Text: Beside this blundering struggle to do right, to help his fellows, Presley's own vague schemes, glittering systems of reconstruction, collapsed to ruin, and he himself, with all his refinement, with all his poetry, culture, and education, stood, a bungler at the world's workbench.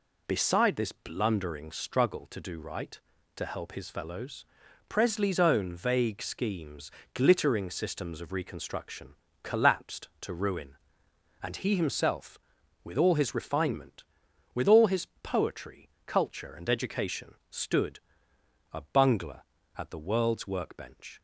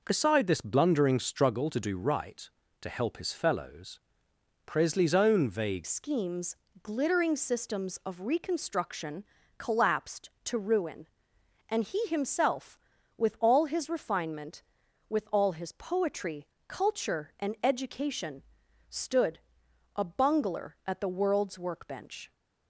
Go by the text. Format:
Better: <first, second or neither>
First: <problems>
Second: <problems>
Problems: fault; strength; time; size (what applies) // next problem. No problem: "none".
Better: first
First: none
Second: changes voice at "schemes"; from 5.8 s on; 16.5 s long